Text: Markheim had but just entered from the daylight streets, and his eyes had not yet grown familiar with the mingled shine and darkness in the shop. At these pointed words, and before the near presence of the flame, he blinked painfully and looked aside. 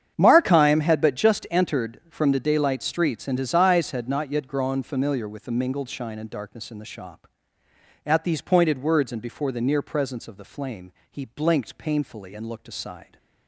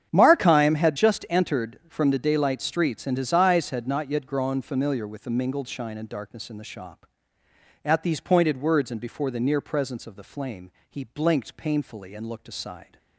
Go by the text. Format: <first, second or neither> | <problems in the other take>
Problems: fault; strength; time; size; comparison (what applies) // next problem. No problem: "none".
first | starts louder than the rest; strong; until 1.1 s; 8.5 dB; strong in the first // skips "but"; at 0.9 s